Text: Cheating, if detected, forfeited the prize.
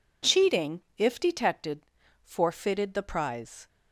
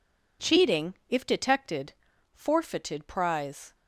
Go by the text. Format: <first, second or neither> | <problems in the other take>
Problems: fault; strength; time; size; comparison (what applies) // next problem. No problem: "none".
first | skips "the"; at 3.0 s